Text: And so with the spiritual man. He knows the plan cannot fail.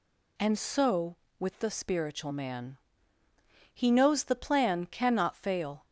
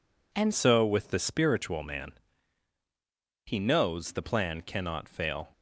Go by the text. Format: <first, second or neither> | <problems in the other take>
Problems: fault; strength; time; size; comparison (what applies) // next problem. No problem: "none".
first | changes voice at "so"; from 0.5 s on; 4.9 s long